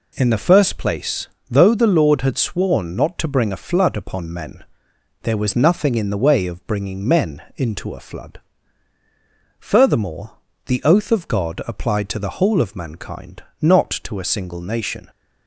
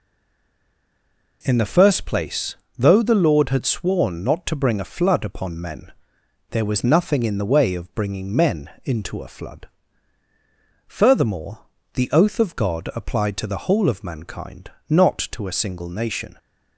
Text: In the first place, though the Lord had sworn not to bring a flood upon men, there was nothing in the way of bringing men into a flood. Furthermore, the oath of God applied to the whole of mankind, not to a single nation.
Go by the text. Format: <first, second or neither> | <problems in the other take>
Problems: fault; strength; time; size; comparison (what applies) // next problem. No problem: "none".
first | stays silent before the first word; noticeable; until 1.4 s; 1.4 s long